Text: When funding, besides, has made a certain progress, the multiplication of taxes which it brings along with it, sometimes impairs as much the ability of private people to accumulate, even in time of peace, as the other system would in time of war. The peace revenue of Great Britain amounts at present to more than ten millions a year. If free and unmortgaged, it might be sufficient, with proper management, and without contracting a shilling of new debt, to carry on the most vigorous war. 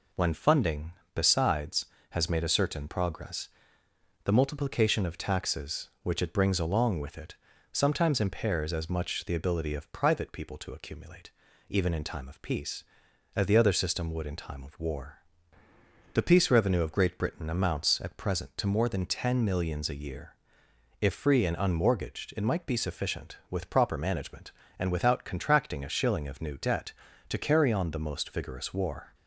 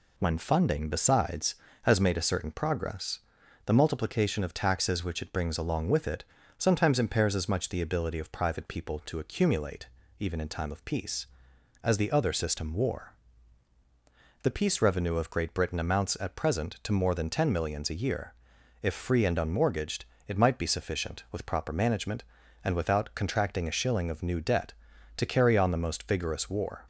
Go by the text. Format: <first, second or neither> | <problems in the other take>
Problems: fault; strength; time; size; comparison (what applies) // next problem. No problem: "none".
first | skips "would in time of"; at 12.7 s